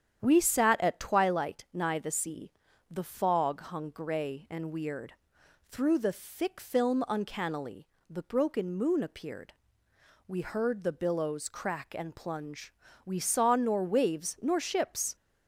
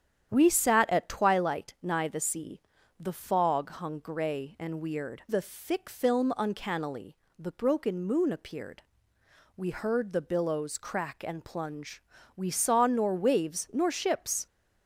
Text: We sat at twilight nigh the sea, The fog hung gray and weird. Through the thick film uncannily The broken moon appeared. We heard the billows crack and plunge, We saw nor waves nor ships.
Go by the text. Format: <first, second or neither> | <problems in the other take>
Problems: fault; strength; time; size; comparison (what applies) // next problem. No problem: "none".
first | starts louder than the rest; strong; until 1.3 s; 9 dB; strong in the first // skips "Through"; at 5.2 s // pauses between "uncannily" and "The"; slight; at 7.1 s; 0.20 s long; slight in the first